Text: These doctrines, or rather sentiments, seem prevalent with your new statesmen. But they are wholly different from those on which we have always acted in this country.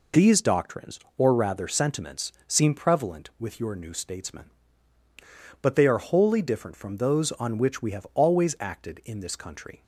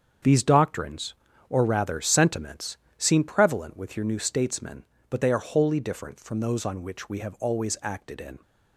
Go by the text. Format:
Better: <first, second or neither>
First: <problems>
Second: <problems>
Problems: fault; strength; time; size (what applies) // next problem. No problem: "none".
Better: first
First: none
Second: starts louder than the rest; strong; until 1.6 s; 7.5 dB // stops before "this country"; at 8.4 s